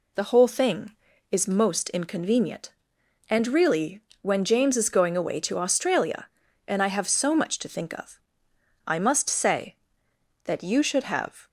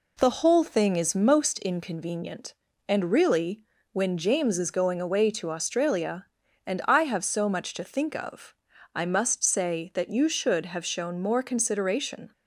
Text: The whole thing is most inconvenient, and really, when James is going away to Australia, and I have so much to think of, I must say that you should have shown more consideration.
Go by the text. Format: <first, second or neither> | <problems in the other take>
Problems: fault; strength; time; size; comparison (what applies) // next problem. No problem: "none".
second | stops before "shown more consideration"; at 11.4 s